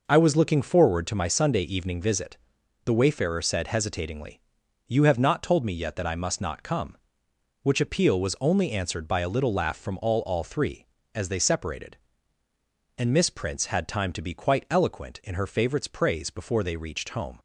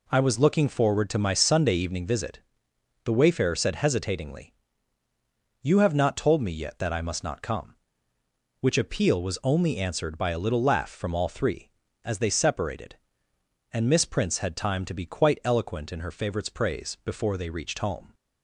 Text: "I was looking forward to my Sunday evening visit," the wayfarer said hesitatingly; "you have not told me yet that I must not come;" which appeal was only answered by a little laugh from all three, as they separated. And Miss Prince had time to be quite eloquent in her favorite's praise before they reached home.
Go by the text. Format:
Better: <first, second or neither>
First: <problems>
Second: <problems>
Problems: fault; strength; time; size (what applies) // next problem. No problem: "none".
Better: second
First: says "all" twice; at 10.2 s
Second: none